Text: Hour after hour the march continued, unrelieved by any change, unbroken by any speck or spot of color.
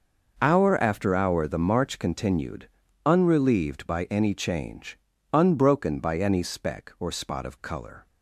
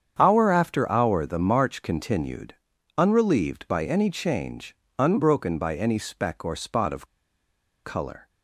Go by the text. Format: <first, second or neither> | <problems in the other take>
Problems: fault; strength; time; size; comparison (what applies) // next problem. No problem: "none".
first | starts louder than the rest; strong; until 1.2 s; 8 dB // pauses between "of" and "color"; noticeable; at 7.0 s; 0.78 s long